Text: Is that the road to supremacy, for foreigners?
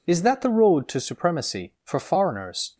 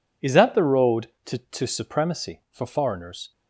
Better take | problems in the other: first | says "to" twice; at 1.3 s

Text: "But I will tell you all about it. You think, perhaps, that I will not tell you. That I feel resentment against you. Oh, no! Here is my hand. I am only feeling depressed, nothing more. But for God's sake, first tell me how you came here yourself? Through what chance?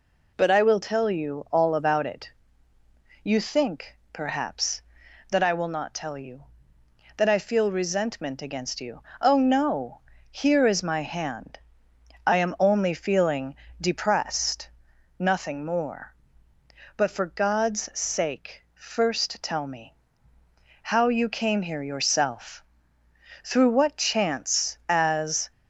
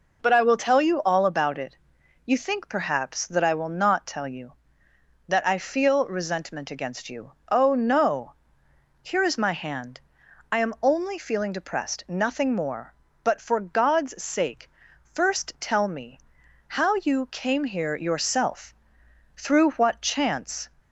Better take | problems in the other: second | pauses between "feeling" and "depressed"; slight; at 13.5 s; 0.26 s long // pauses between "me" and "how"; noticeable; at 19.9 s; 0.86 s long; noticeable in the second // goes on to say "As"; noticeable; from 24.8 s on; 0.62 s long

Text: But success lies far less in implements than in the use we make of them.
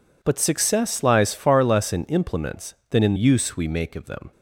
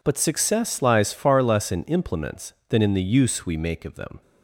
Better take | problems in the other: second | skips "the"; at 3.1 s

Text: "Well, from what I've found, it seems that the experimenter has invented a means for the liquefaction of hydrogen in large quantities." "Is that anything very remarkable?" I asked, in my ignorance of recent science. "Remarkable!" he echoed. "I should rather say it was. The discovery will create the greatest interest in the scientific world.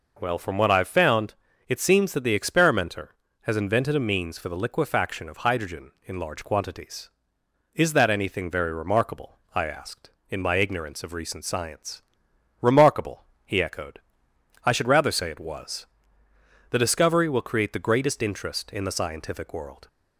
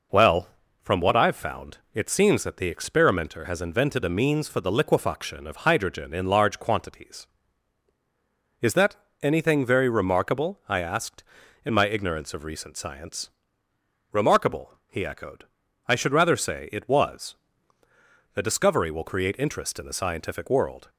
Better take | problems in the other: first | pauses between "that" and "anything"; slight; at 8.9 s; 0.28 s long // skips "the greatest"; at 19.3 s

